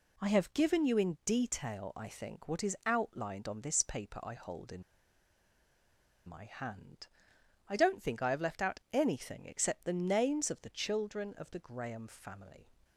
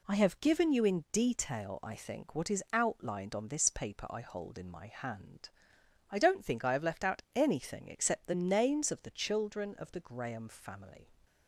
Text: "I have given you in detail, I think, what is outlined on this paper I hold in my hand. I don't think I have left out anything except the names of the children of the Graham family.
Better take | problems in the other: second | pauses between "in" and "my"; strong; at 4.8 s; 1.4 s long

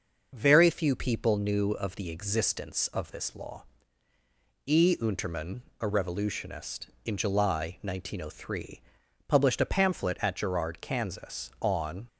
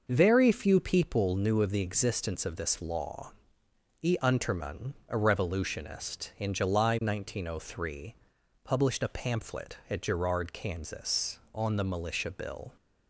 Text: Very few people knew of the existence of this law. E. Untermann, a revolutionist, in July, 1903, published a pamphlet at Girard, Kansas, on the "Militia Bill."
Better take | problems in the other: second | stops before "the Militia Bill"; at 12.0 s

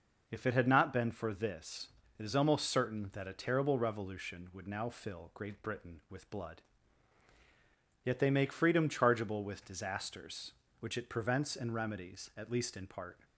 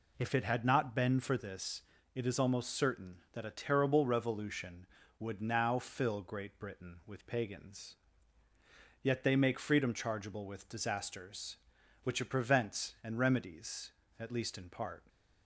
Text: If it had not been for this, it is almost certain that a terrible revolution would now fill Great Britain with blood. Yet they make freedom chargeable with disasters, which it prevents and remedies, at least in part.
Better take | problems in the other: first | says "pagans" for "blood"; at 7.2 s

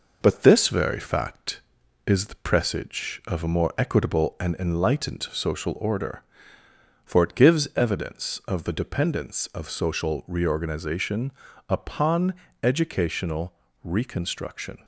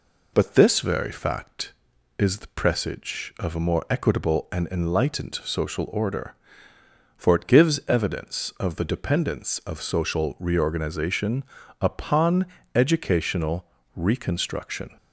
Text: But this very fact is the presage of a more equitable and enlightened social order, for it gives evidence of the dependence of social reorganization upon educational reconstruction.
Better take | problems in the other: second | gets quieter; slight; throughout; 2.5 dB // pauses between "reorganization" and "upon"; slight; at 11.3 s; 0.36 s long; slight in the second // pauses between "upon" and "educational"; slight; at 12.3 s; 0.28 s long; slight in the second // pauses between "educational" and "reconstruction"; slight; at 13.5 s; 0.30 s long; slight in the second

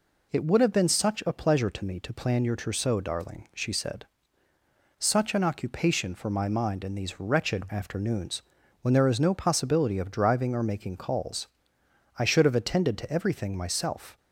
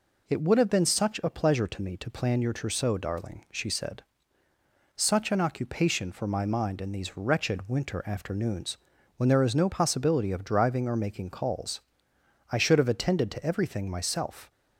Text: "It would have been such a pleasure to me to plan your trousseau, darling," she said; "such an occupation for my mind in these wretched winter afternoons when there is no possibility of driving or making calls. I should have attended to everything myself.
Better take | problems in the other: second | skips "winter"; at 7.7 s // pauses between "afternoons" and "when"; at 8.4 s; 0.42 s long; also in the second

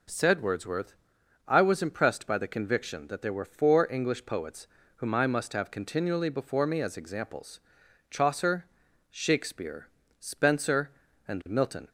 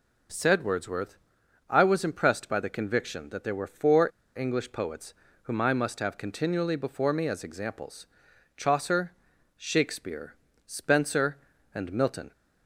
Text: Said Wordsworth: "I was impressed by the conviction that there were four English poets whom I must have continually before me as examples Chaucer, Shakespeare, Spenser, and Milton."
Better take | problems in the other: first | pauses between "four" and "English"; slight; at 4.0 s; 0.30 s long // pauses between "poets" and "whom"; slight; at 5.1 s; 0.30 s long; slight in the first // pauses between "examples" and "Chaucer"; noticeable; at 8.0 s; 0.50 s long; noticeable in the first

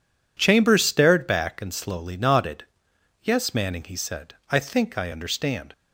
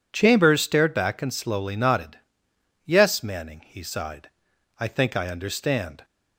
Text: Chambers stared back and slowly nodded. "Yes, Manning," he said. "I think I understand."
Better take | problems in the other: first | says "sighed" for "said"; at 3.8 s

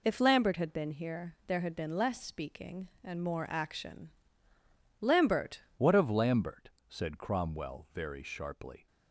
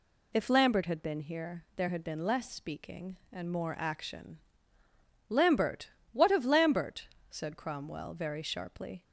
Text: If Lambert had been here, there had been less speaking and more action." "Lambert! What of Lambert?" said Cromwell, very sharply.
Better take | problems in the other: second | changes voice at "What"; from 5.7 s on; 3.1 s long

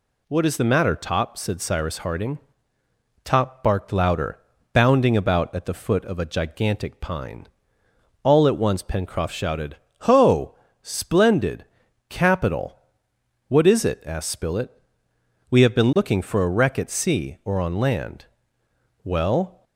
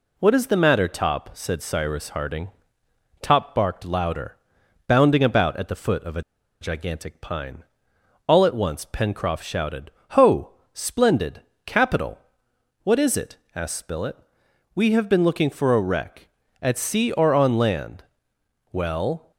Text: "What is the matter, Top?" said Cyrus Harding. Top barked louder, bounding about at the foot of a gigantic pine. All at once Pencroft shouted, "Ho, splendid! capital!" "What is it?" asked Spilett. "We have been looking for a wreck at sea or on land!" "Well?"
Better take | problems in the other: first | pauses between "a" and "gigantic"; at 6.2 s; 0.38 s long

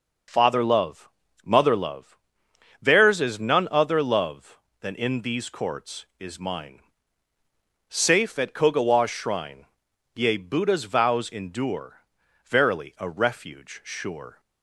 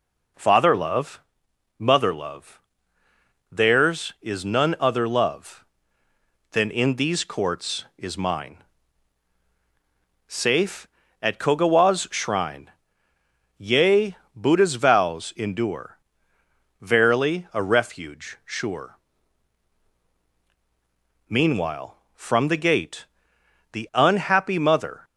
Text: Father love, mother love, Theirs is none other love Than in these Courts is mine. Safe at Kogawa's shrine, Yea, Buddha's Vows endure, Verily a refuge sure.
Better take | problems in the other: first | goes on to say "Meanwhile from the gate the unhappy mother"; strong; from 21.2 s on; 3.7 s long

